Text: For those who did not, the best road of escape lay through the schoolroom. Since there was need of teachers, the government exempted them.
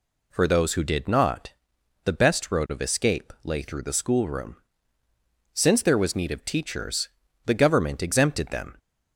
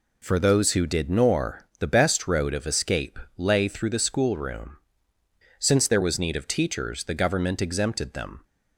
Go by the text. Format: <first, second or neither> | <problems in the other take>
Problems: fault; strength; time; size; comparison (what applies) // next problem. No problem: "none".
first | says "nor" for "not"; at 1.0 s // pauses between "escape" and "lay"; slight; at 3.1 s; 0.20 s long